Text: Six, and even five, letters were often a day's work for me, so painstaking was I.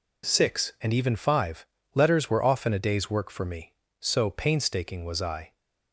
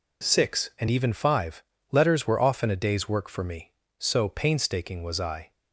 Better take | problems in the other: neither | none

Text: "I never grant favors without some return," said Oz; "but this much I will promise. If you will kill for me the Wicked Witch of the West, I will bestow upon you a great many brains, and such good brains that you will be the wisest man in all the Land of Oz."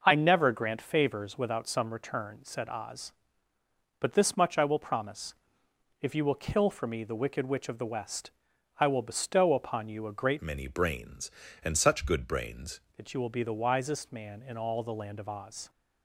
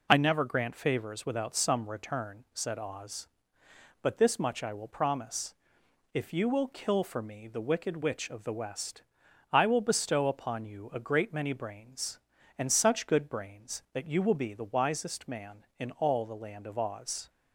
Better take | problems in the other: second | changes voice from "many" to "brains"; from 10.4 to 12.8 s; 2.4 s long

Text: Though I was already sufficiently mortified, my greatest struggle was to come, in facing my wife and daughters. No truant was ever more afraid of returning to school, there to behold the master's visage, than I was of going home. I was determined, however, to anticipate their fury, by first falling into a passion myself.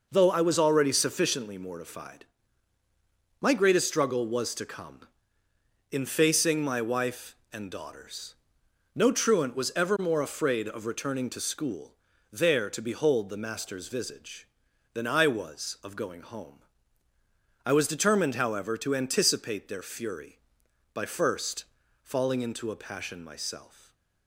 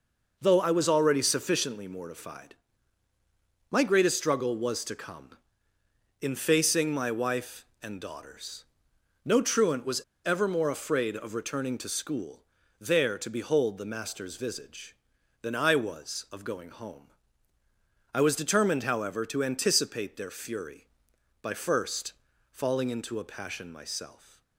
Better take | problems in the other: first | pauses between "was" and "ever"; slight; at 9.9 s; 0.26 s long // pauses between "first" and "falling"; slight; at 22.1 s; 0.36 s long; slight in the first

